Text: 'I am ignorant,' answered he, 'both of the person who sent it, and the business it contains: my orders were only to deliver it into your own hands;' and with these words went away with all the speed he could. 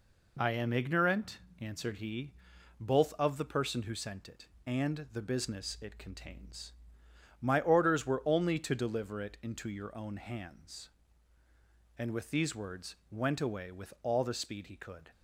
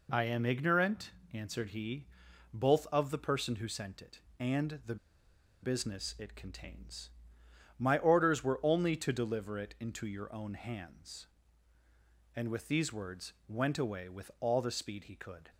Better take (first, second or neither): first